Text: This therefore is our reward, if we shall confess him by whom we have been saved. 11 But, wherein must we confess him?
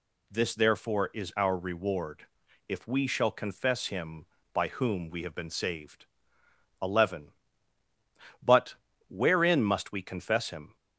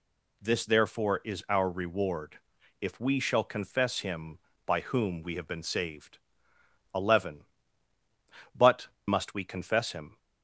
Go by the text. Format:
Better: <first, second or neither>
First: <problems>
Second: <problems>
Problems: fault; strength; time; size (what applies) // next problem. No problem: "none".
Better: first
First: none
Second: skips "wherein"; at 8.9 s